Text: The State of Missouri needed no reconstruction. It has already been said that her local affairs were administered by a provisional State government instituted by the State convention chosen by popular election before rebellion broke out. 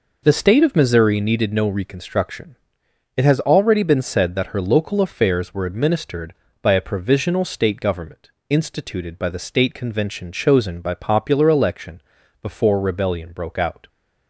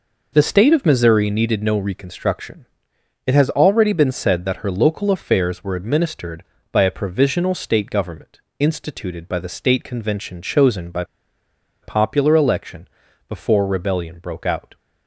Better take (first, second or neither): first